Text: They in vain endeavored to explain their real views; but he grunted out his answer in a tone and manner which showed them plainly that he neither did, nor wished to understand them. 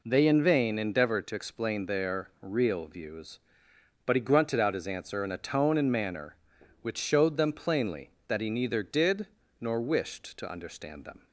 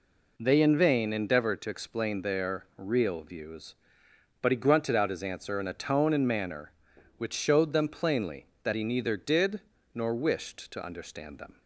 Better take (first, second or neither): neither